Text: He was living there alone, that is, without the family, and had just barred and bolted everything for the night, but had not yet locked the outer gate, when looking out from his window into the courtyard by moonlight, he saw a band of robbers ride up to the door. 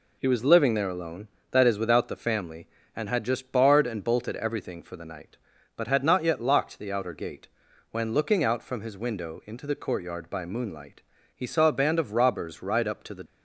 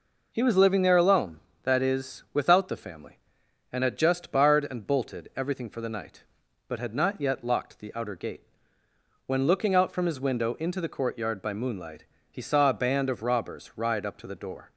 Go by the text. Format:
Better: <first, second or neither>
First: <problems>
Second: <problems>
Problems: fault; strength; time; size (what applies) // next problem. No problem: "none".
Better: second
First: stops before "door"; at 13.2 s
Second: none